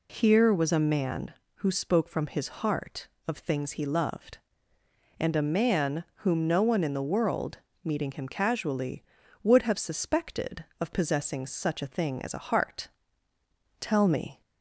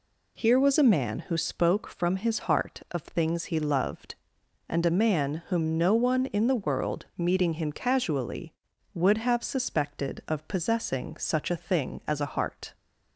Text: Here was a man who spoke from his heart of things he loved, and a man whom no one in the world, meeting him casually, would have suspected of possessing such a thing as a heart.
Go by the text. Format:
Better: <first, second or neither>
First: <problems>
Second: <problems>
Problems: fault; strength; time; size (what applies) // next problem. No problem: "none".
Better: second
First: goes on to say "Tell me"; noticeable; from 13.7 s on; 0.62 s long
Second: none